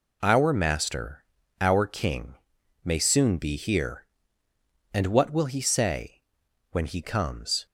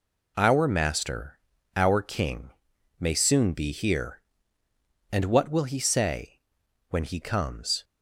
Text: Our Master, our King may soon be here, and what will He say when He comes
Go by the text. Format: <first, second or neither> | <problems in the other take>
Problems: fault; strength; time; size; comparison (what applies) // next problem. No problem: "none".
neither | pauses between "King" and "may"; noticeable; the same in both // pauses between "say" and "when"; noticeable; the same in both